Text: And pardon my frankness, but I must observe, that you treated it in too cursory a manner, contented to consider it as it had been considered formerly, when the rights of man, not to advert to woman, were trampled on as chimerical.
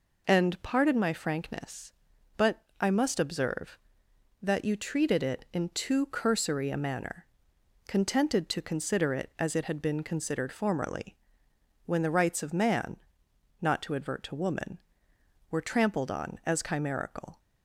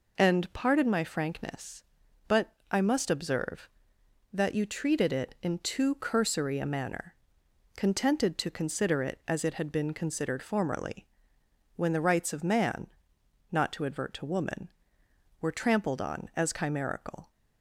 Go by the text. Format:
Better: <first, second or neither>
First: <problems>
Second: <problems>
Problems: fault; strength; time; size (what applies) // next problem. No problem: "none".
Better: neither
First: pauses between "but" and "I"; slight; at 2.6 s; 0.18 s long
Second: pauses between "but" and "I"; slight; at 2.5 s; 0.18 s long